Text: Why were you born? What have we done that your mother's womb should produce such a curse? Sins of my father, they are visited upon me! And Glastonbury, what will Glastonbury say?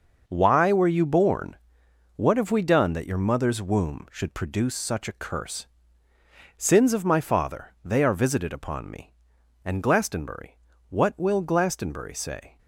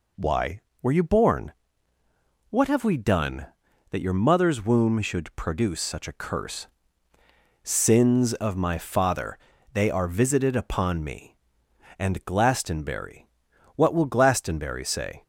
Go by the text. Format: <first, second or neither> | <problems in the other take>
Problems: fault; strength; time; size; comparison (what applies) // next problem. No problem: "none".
second | gets quieter; strong; throughout; 9 dB